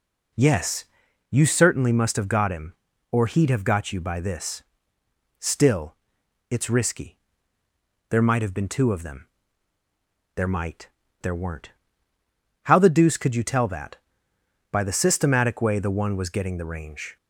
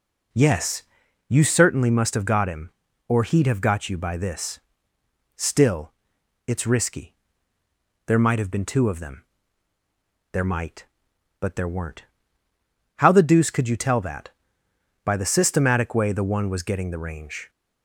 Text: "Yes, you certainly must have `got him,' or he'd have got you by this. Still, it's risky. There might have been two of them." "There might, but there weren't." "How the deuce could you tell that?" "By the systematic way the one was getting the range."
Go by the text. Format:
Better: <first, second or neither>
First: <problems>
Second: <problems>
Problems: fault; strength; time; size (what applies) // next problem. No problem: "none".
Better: second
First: skips "but"; at 11.0 s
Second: none